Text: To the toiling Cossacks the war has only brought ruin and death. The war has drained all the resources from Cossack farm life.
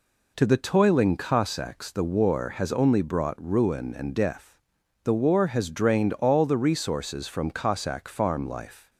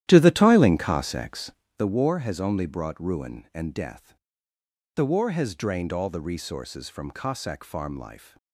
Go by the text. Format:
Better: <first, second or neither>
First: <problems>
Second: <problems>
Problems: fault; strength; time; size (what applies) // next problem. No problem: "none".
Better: first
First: none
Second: starts louder than the rest; strong; until 1.7 s; 12 dB // pauses between "Cossacks" and "the"; slight; at 1.5 s; 0.28 s long